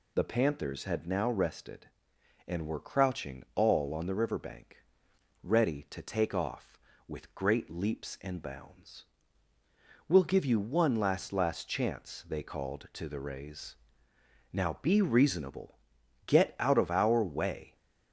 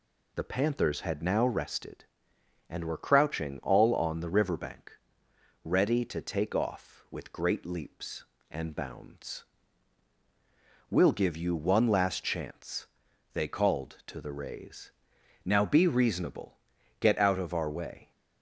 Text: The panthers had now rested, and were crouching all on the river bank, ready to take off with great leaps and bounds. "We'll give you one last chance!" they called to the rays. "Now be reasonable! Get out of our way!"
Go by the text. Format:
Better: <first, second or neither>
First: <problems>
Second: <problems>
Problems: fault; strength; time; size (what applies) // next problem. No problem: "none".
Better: second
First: says "last" twice; at 11.3 s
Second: none